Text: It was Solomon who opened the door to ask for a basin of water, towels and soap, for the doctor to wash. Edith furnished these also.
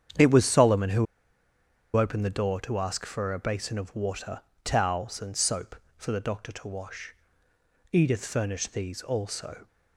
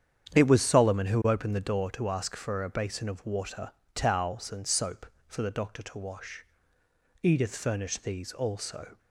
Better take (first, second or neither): second